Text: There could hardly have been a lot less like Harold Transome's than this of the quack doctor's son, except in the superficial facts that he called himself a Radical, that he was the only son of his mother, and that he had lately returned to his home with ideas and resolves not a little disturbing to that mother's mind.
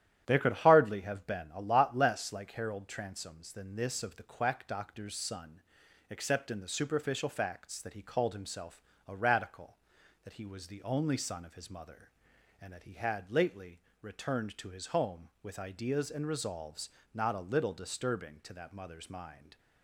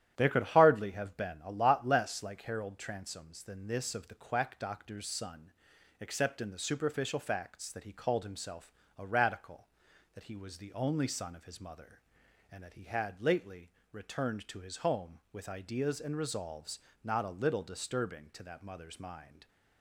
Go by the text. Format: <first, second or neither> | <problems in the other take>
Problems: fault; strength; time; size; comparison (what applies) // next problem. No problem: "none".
neither | starts louder than the rest; strong; the same in both // pauses between "himself" and "a"; slight; the same in both // pauses between "lately" and "returned"; slight; the same in both // pauses between "resolves" and "not"; slight; the same in both